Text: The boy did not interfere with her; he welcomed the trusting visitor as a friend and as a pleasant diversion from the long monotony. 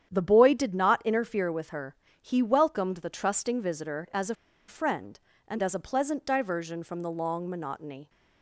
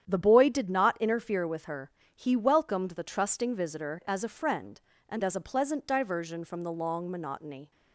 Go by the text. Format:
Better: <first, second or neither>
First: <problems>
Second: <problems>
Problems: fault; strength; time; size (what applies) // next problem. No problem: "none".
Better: second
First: starts louder than the rest; strong; until 1.1 s; 9.5 dB // pauses between "a" and "friend"; slight; at 4.3 s; 0.33 s long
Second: starts louder than the rest; strong; until 1.0 s; 9.5 dB